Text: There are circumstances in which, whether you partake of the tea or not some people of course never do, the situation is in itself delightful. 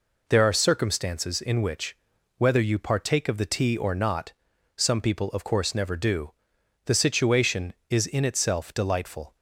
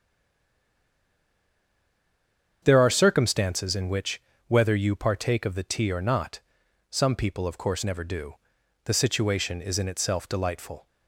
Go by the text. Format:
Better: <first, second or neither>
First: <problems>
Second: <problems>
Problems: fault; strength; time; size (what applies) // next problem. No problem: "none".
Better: first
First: pauses between "not" and "some"; at 4.3 s; 0.44 s long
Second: stays silent before the first word; strong; until 2.6 s; 2.6 s long // starts louder than the rest; strong; until 3.6 s; 7.5 dB // pauses between "not" and "some"; noticeable; at 6.4 s; 0.50 s long